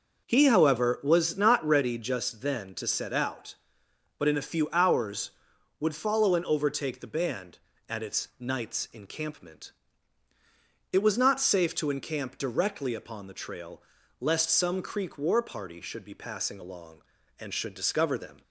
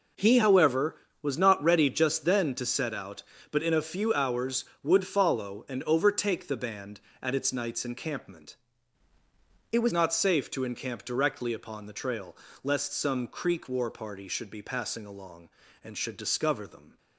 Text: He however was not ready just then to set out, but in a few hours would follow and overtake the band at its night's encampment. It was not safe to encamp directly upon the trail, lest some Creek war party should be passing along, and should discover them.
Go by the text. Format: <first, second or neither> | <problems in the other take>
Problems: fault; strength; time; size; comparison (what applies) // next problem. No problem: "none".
first | changes voice from "It" to "was"; from 9.7 to 9.9 s; 0.2 s long